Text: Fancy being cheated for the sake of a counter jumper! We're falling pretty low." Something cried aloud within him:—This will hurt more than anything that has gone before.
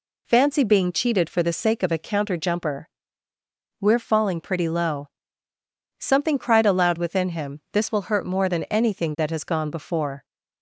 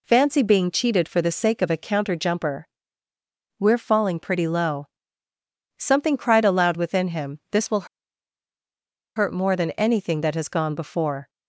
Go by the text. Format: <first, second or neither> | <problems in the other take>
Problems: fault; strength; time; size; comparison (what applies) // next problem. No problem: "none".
first | pauses between "will" and "hurt"; strong; at 7.8 s; 1.2 s long